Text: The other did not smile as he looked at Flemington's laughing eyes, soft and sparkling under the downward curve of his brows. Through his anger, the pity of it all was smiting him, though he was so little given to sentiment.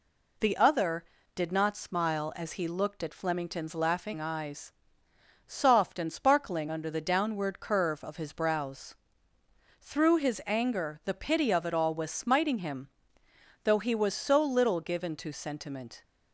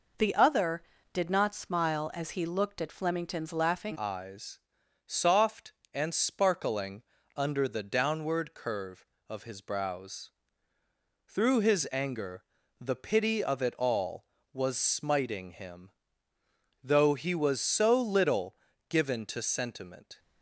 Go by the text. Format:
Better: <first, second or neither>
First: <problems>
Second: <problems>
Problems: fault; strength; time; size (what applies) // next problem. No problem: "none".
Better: first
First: none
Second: changes voice at "eyes"; from 3.9 s on; 16.2 s long // pauses between "sparkling" and "under"; slight; at 7.0 s; 0.34 s long // pauses between "little" and "given"; slight; at 18.5 s; 0.34 s long